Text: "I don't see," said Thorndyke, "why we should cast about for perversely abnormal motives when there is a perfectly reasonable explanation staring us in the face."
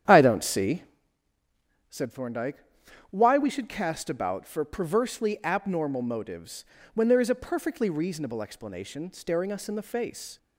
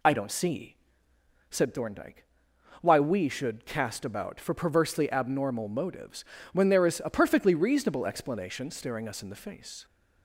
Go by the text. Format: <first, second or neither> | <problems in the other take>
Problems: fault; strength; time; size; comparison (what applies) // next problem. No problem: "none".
second | starts louder than the rest; strong; until 1.0 s; 9.5 dB // pauses between "motives" and "when"; slight; at 6.6 s; 0.30 s long; slight in the second